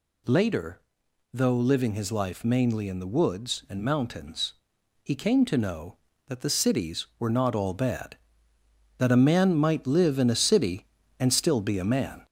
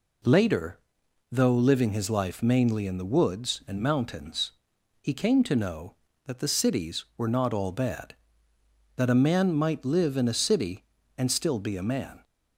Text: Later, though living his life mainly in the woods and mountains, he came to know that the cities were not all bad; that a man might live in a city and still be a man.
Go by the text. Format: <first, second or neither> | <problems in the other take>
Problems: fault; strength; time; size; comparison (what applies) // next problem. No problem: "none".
second | gets louder; slight; throughout; 3.5 dB